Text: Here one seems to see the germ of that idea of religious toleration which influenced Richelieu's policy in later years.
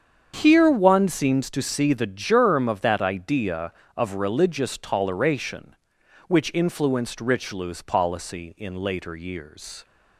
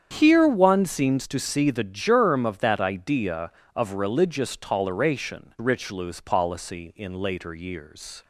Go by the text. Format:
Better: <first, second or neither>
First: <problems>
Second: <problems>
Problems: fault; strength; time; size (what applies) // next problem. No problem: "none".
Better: first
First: starts louder than the rest; strong; until 1.4 s; 8 dB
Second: starts louder than the rest; strong; until 1.2 s; 8.5 dB // skips "which influenced"; at 5.5 s